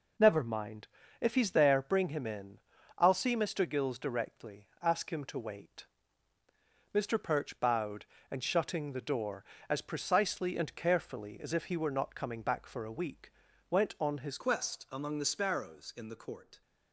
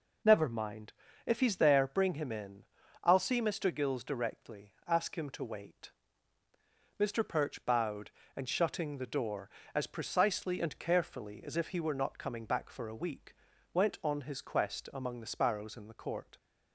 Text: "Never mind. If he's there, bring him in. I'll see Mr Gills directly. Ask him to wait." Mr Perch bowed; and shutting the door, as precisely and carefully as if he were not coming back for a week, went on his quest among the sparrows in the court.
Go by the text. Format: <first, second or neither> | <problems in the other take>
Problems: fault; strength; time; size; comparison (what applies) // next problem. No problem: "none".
second | changes voice at "quest"; from 14.3 s on; 2.3 s long